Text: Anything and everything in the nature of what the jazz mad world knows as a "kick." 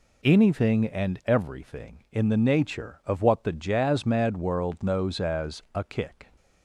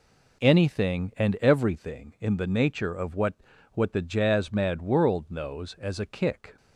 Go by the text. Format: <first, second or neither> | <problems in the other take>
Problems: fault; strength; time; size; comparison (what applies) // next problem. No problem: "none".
first | says "what" twice; at 3.7 s